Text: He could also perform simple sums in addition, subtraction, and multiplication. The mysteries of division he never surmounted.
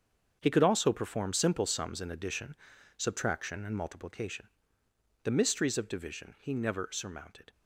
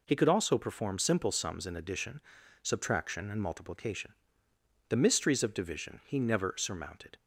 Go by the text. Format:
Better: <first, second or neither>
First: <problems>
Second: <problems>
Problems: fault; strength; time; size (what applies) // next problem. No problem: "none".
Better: second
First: gets quieter; strong; throughout; 11.5 dB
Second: none